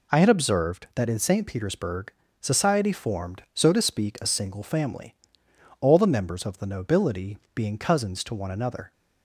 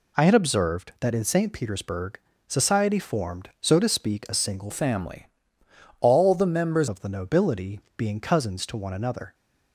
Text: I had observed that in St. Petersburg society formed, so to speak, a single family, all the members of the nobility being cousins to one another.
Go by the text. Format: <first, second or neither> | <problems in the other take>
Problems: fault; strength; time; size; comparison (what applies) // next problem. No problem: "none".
first | pauses between "Petersburg" and "society"; slight; at 2.1 s; 0.26 s long; slight in the first // changes voice from "family" to "members"; from 4.7 to 6.8 s; 2.1 s long // pauses between "nobility" and "being"; slight; at 7.8 s; 0.16 s long; slight in the first